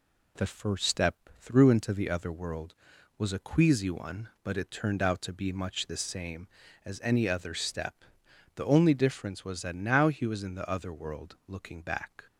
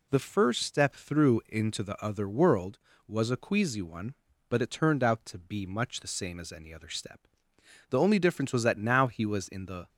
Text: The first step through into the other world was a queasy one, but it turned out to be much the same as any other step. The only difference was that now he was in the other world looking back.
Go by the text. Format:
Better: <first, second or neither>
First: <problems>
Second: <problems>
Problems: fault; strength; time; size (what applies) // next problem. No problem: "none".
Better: first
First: none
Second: stops before "other world looking back"; at 9.8 s